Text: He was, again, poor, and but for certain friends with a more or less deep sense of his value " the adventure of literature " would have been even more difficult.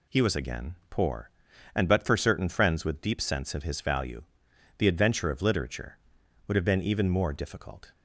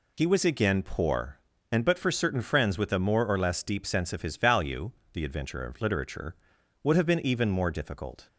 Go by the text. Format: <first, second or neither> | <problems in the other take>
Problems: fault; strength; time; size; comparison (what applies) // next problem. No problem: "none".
second | skips "a more or less"; at 3.0 s